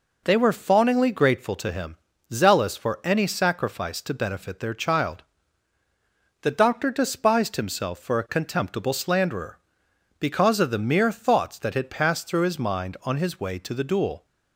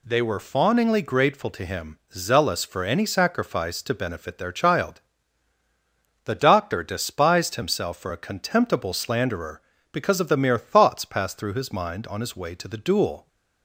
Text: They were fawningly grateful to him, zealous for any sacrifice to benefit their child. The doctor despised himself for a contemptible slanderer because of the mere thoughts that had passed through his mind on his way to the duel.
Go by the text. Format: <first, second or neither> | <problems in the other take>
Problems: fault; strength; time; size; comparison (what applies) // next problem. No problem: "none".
first | skips "that had"; at 11.0 s